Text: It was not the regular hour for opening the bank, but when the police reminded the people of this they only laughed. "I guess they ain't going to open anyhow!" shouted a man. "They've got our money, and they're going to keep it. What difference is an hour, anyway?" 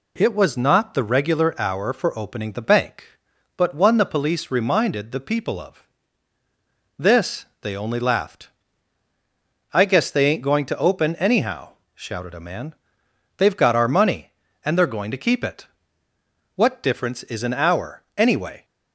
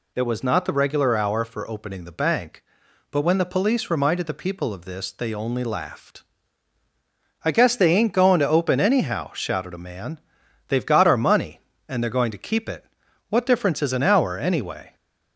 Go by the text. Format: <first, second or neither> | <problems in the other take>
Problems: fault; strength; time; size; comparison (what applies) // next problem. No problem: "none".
second | says "one" for "when"; at 3.7 s // pauses between "of" and "this"; at 5.8 s; 1.1 s long // pauses between "this" and "they"; slight; at 7.4 s; 0.16 s long